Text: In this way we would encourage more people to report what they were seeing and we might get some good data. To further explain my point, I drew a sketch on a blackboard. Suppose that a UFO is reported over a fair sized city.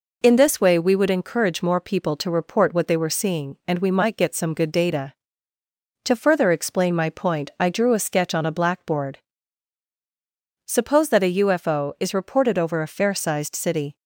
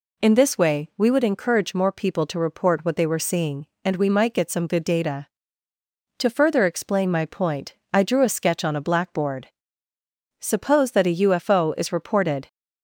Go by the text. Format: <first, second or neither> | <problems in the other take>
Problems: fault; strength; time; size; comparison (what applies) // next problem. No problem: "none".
first | stops before "over a fair sized city"; at 12.4 s